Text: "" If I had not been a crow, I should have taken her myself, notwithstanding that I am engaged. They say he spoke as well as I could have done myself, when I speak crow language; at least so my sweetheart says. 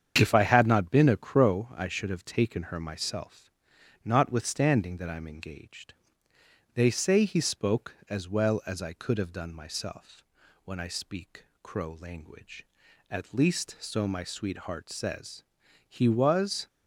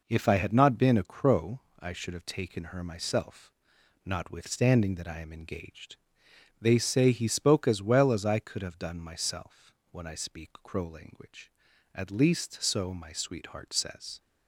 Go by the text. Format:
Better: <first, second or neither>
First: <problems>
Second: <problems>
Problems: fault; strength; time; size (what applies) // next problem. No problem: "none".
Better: second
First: starts louder than the rest; strong; until 1.1 s; 8 dB // pauses between "speak" and "crow"; slight; at 11.4 s; 0.16 s long // goes on to say "He was"; noticeable; from 15.8 s on; 0.80 s long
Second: none